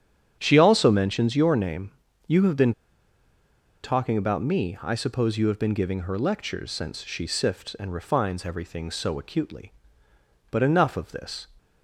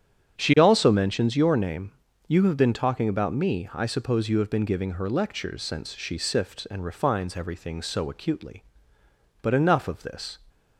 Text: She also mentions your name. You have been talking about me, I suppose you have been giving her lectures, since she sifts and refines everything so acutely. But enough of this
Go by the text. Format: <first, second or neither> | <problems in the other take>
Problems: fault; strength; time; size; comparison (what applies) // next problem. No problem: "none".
second | starts louder than the rest; strong; until 1.4 s; 9 dB; strong in the second // pauses between "been" and "talking"; at 2.7 s; 1.1 s long